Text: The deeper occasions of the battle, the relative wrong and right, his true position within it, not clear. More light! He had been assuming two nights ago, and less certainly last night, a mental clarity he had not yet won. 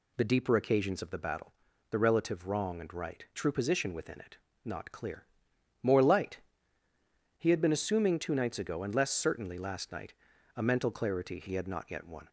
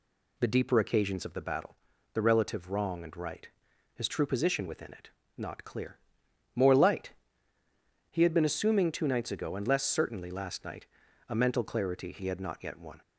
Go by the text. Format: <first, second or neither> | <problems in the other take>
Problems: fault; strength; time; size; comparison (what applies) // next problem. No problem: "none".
second | skips "his"; at 3.3 s